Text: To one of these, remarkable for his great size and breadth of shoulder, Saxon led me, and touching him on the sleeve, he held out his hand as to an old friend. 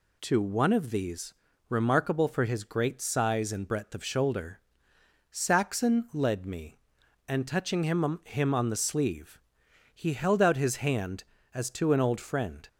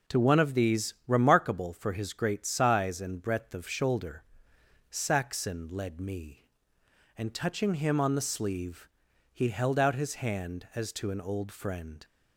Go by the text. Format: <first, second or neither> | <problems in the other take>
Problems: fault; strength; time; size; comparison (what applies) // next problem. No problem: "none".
second | says "him" twice; at 8.2 s